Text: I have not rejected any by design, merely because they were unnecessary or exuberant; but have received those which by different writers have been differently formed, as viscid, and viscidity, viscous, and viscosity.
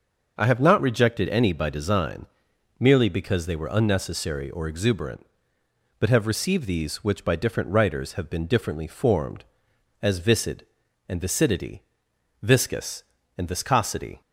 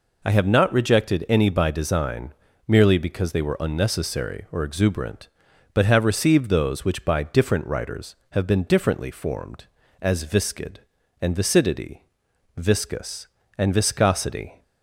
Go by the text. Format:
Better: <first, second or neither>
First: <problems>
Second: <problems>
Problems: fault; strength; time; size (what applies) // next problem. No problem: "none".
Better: second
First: starts louder than the rest; until 1.3 s; 6.5 dB // says "these" for "those"; at 6.6 s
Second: none